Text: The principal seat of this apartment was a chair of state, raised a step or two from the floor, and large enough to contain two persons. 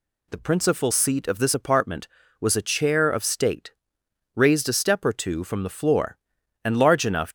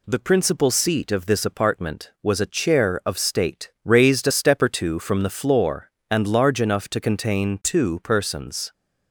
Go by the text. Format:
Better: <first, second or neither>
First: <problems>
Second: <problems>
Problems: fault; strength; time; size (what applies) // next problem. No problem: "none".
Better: second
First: stops before "to contain two persons"; at 7.2 s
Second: none